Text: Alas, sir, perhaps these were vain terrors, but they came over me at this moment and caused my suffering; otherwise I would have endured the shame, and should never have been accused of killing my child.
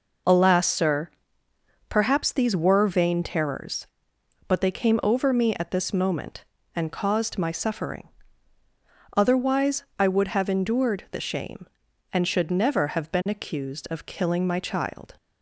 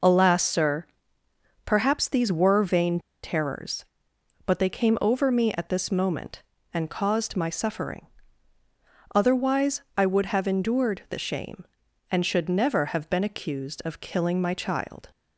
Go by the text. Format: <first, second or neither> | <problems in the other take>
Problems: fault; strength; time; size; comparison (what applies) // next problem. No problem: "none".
first | pauses between "vain" and "terrors"; slight; at 2.9 s; 0.25 s long // pauses between "otherwise" and "I"; slight; at 9.8 s; 0.16 s long; slight in the first